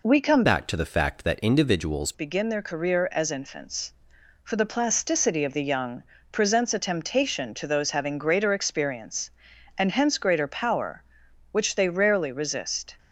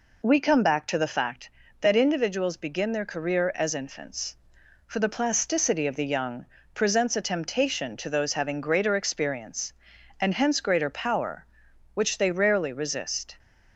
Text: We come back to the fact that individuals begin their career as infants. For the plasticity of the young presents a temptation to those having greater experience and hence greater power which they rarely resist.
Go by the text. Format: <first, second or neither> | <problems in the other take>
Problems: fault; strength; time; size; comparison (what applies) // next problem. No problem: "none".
second | changes voice from "back" to "individuals"; from 0.4 to 2.1 s; 1.7 s long // pauses between "young" and "presents"; slight; at 6.0 s; 0.28 s long; slight in the second